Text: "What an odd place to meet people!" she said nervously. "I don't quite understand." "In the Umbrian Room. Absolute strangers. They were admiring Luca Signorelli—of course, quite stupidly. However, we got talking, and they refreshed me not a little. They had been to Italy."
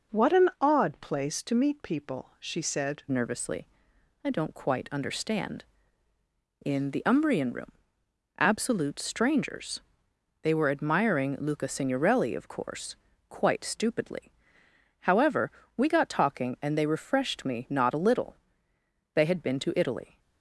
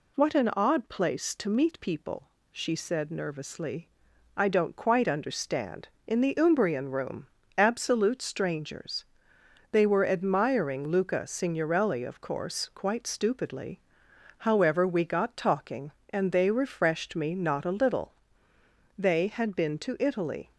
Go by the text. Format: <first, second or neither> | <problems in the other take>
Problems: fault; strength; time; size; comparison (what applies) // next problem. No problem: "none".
second | changes voice at "nervously"; from 3.0 s on; 17.1 s long